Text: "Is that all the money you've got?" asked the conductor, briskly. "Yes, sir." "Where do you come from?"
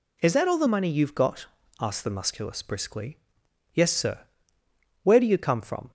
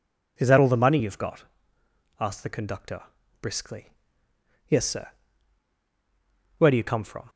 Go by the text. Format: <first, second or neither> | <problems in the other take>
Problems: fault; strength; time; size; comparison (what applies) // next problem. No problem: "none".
second | says "musculus" for "conductor"; at 2.1 s